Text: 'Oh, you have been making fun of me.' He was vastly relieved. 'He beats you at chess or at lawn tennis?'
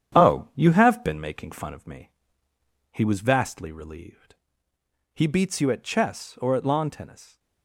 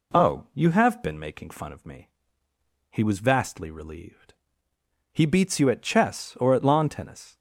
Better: second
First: gets quieter; noticeable; throughout; 4.5 dB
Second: none

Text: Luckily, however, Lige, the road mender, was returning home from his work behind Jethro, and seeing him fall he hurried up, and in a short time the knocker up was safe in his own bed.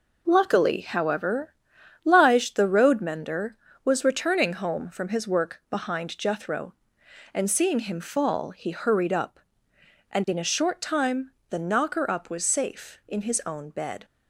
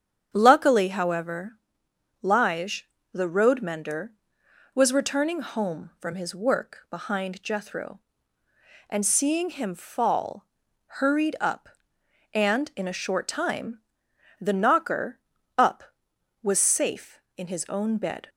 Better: first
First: pauses between "time" and "the"; slight; at 11.3 s; 0.18 s long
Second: starts louder than the rest; strong; until 1.3 s; 8.5 dB // skips "he"; at 10.6 s // pauses between "time" and "the"; noticeable; at 13.7 s; 0.62 s long // pauses between "knocker" and "up"; at 15.1 s; 0.40 s long

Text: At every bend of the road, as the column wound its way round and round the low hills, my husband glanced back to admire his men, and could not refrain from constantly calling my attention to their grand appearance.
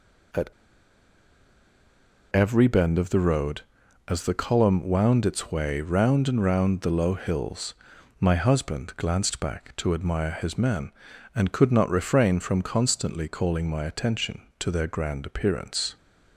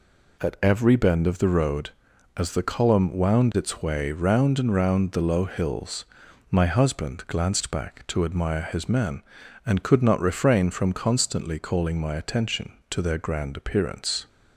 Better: second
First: pauses between "At" and "every"; strong; at 0.5 s; 1.8 s long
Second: none

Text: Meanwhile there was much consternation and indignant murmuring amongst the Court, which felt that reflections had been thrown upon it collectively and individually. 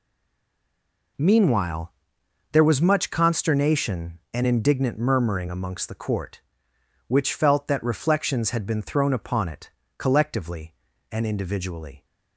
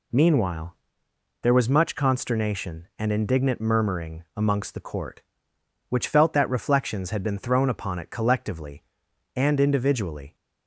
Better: second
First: stays silent before the first word; noticeable; until 1.1 s; 1.1 s long // pauses between "Meanwhile" and "there"; noticeable; at 1.9 s; 0.58 s long // pauses between "it" and "collectively"; slight; at 9.6 s; 0.28 s long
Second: pauses between "Meanwhile" and "there"; noticeable; at 0.7 s; 0.68 s long

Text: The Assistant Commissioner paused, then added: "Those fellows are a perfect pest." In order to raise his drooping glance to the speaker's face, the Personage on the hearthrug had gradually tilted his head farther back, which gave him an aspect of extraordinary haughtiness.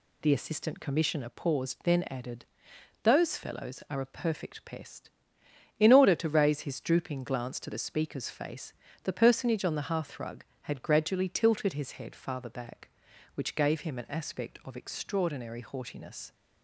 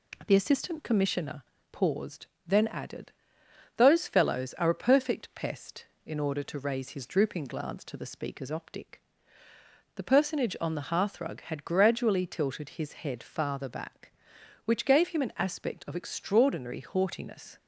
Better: first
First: none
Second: pauses between "Commissioner" and "paused"; slight; at 1.4 s; 0.30 s long // says "optic" for "face"; at 8.5 s

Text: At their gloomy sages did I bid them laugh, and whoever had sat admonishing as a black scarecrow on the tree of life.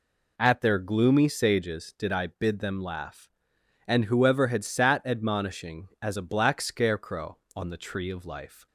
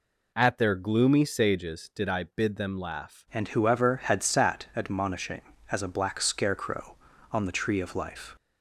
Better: first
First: none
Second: changes voice at "and"; from 3.3 s on; 5.0 s long

